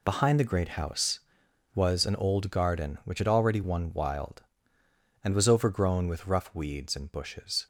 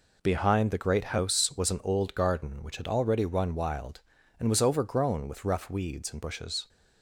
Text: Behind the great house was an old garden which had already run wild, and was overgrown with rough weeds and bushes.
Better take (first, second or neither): second